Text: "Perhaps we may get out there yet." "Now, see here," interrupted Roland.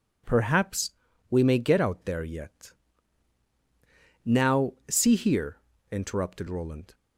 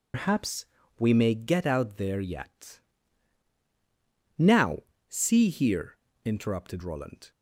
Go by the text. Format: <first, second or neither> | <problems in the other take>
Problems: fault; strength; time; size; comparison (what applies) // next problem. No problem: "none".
first | loses the start of "Perhaps"; at 0.1 s; 155 ms // pauses between "Perhaps" and "we"; slight; at 0.6 s; 0.34 s long; also in the first